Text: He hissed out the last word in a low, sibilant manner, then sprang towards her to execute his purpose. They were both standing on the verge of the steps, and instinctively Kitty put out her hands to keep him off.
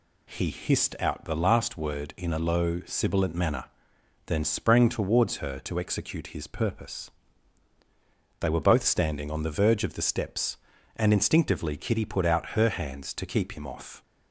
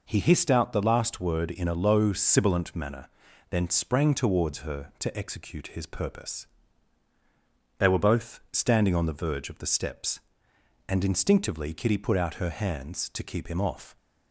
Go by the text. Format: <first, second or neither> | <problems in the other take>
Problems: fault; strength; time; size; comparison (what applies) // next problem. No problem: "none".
neither | none